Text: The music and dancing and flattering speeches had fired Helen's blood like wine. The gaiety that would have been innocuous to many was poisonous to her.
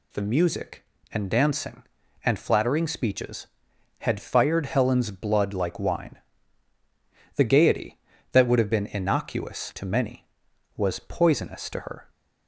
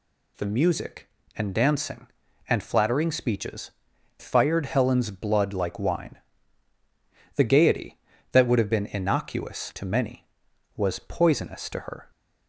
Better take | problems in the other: first | skips "had"; at 3.9 s

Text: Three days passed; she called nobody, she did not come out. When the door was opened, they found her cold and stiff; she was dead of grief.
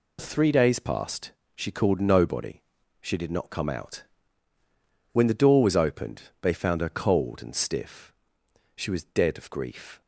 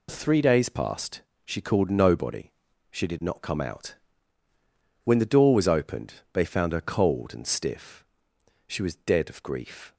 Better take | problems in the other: neither | none

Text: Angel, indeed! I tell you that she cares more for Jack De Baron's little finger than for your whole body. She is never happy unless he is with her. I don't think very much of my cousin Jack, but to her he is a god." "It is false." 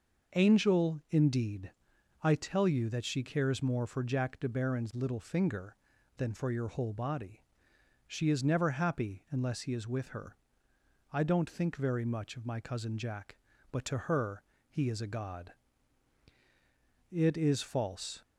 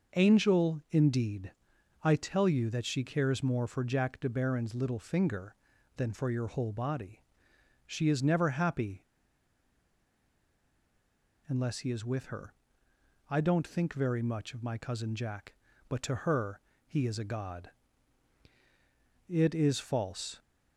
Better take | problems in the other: first | pauses between "happy" and "unless"; strong; at 9.0 s; 2.4 s long // pauses between "her" and "he"; slight; at 16.6 s; 0.26 s long; slight in the first

